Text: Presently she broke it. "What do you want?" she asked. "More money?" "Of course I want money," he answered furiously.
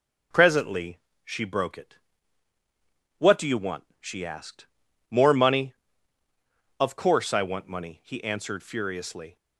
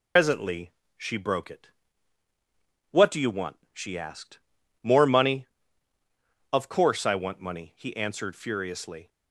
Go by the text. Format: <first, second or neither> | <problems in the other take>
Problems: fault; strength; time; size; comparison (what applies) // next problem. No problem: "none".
first | loses the start of "Presently"; at 0.1 s; 110 ms // pauses between "Presently" and "she"; slight; at 0.7 s; 0.28 s long; slight in the first